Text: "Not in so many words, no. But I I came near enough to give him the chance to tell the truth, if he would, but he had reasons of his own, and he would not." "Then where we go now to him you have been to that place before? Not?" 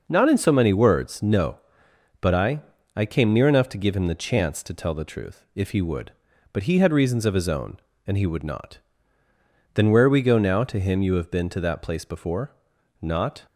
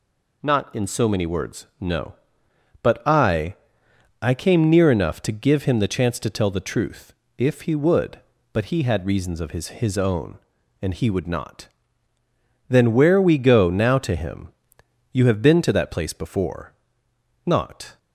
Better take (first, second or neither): first